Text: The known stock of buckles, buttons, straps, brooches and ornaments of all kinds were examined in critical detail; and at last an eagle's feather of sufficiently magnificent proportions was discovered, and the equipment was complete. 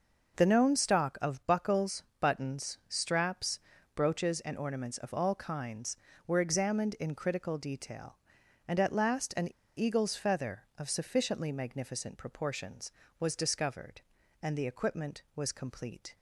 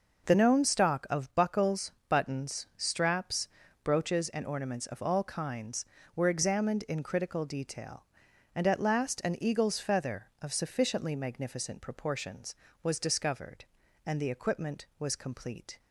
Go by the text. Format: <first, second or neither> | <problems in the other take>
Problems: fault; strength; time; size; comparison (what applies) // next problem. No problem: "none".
second | pauses between "an" and "eagle's"; slight; at 9.4 s; 0.31 s long